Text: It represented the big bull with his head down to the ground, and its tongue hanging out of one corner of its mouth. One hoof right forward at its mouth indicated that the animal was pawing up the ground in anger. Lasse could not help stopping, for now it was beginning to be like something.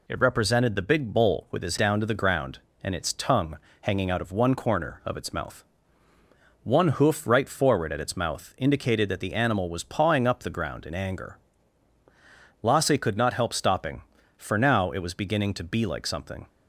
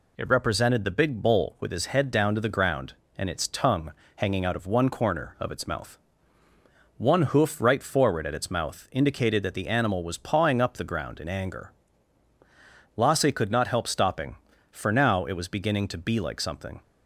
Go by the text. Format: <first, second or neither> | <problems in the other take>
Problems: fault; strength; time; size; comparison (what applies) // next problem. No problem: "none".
second | skips "head"; at 1.7 s // pauses between "tongue" and "hanging"; slight; at 3.5 s; 0.26 s long; slight in the second